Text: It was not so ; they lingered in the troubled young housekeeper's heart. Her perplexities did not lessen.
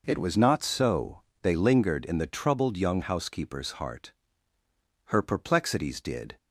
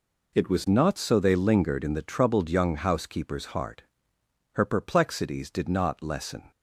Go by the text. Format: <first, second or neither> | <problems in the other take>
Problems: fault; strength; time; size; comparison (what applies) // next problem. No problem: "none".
second | stops before "not lessen"; at 6.3 s